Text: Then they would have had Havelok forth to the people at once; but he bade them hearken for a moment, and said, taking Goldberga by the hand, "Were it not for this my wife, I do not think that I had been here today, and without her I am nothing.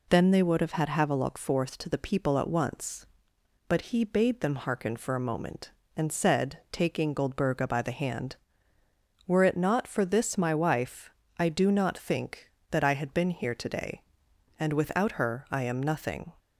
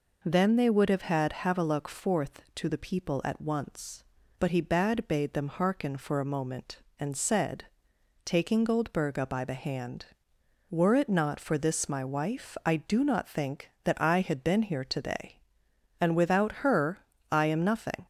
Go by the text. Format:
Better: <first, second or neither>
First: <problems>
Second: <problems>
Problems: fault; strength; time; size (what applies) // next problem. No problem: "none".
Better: first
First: none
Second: says "bade" twice; at 5.0 s // pauses between "her" and "I"; slight; at 16.9 s; 0.32 s long